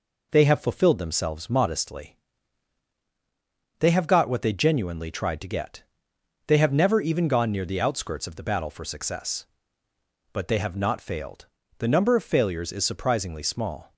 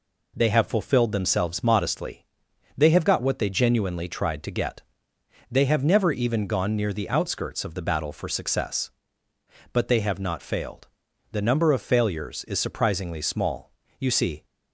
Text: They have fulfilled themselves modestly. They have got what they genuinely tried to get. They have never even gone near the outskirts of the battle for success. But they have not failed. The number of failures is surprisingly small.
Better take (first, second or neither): first